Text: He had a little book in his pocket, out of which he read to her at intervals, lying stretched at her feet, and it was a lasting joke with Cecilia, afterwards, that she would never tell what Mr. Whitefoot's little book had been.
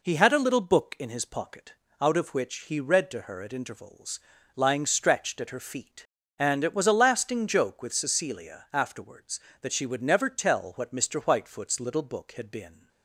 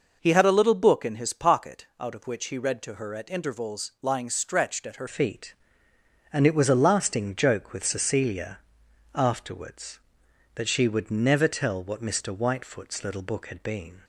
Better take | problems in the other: first | changes voice at "feet"; from 5.0 s on; 9.0 s long

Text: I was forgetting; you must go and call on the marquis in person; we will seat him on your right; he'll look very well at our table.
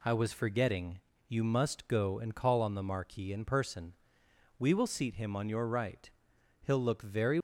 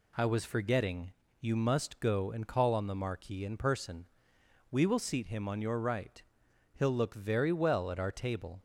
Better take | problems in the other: second | stops before "well at our table"; at 7.3 s

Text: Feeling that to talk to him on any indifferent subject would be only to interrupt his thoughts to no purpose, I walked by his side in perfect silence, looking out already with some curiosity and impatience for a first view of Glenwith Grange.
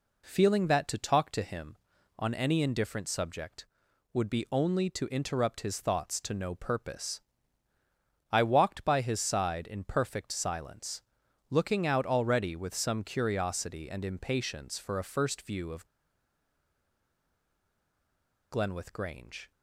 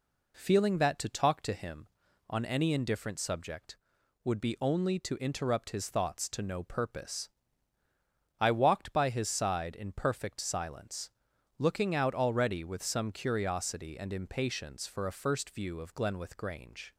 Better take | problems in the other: second | pauses between "of" and "Glenwith"; strong; at 15.8 s; 2.6 s long

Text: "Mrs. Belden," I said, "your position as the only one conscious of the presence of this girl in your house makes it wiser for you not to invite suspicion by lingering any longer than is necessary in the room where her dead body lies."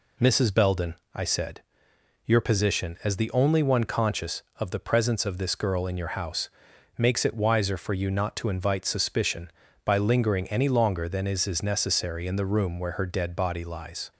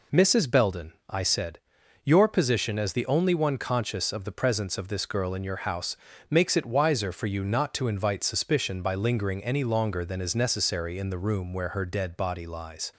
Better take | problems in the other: second | pauses between "house" and "makes"; noticeable; at 6.4 s; 0.46 s long; slight in the second // says "is" twice; at 11.4 s

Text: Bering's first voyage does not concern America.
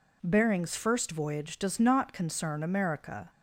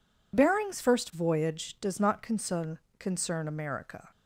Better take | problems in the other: first | says "concern" twice; at 2.9 s

